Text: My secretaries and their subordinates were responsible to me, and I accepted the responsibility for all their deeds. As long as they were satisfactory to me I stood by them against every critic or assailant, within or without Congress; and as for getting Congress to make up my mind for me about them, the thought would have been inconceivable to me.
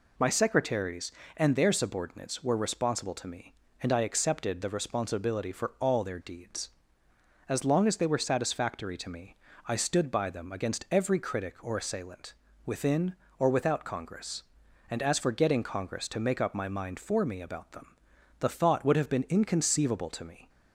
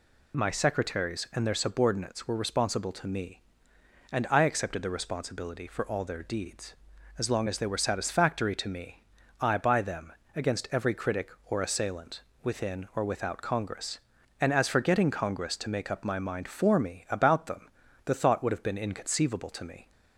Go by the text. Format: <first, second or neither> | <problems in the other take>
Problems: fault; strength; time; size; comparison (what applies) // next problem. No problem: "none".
first | pauses between "me" and "I"; slight; at 9.0 s; 0.36 s long; slight in the first // skips "stood"; at 9.5 s // pauses between "them" and "against"; slight; at 10.1 s; 0.24 s long